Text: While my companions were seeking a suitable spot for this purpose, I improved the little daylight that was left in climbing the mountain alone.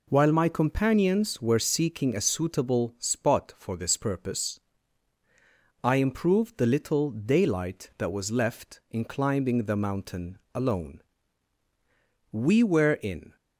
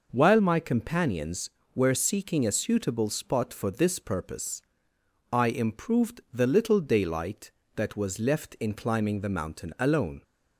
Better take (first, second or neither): second